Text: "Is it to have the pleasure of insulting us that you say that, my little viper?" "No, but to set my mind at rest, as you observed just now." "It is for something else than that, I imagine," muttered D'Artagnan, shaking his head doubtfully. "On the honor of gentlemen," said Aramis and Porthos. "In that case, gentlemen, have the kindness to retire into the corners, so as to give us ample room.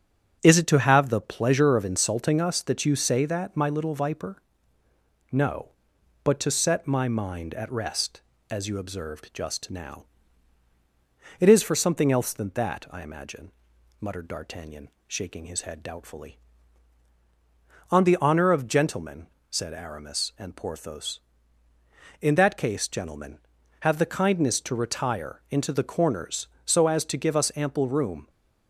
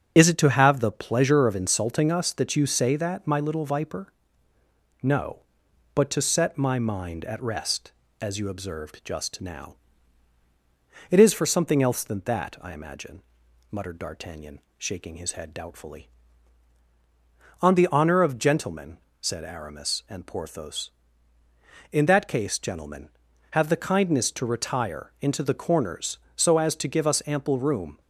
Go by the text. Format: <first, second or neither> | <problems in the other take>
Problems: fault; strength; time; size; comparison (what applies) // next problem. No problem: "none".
first | loses the start of "Is"; at 0.1 s; 40 ms // starts louder than the rest; strong; until 1.1 s; 7 dB; strong in the first